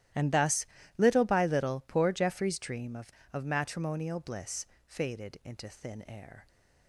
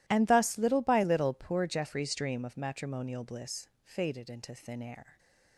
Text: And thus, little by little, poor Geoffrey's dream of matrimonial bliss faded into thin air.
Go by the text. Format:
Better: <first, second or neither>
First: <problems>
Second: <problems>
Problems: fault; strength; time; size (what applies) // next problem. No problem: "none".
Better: second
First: starts louder than the rest; strong; until 1.4 s; 13.5 dB // says "of" twice; at 3.3 s // pauses between "bliss" and "faded"; slight; at 4.6 s; 0.20 s long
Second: pauses between "bliss" and "faded"; slight; at 3.6 s; 0.16 s long